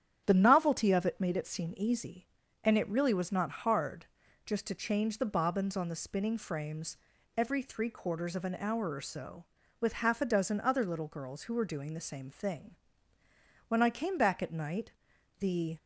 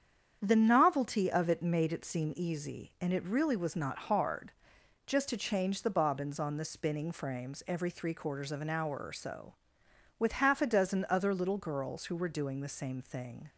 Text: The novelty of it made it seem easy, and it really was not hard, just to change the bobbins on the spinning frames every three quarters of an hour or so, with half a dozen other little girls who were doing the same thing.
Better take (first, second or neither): second